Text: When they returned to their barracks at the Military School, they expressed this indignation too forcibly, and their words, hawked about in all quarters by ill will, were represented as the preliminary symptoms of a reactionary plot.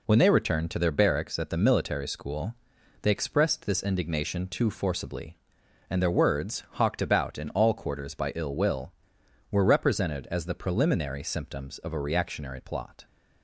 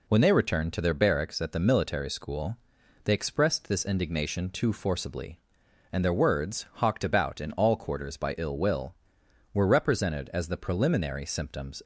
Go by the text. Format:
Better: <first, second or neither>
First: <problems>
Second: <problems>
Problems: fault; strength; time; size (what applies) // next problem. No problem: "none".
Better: first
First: none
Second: stops before "of a reactionary plot"; at 11.8 s